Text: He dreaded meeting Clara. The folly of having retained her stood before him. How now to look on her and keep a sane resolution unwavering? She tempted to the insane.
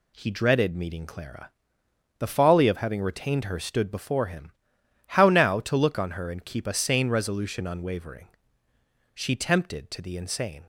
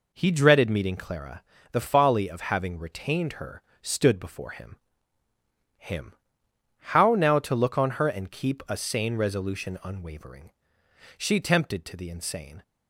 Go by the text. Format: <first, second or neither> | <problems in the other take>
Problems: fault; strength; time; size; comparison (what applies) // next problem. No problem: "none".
first | pauses between "her" and "stood"; slight; at 3.6 s; 0.18 s long // says "him" twice; at 5.7 s